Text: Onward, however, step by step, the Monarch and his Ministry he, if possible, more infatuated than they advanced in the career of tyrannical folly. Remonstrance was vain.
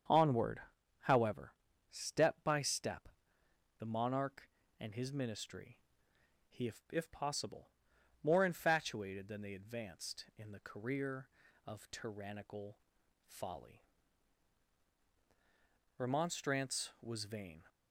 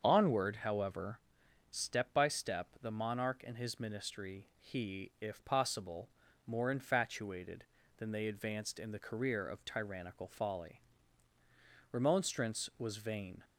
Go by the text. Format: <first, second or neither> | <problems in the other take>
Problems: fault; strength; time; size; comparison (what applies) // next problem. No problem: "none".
second | starts louder than the rest; strong; until 1.4 s; 7.5 dB; strong in the second // pauses between "Ministry" and "he"; noticeable; at 5.7 s; 0.70 s long // says "if" twice; at 6.9 s // pauses between "tyrannical" and "folly"; noticeable; at 12.7 s; 0.48 s long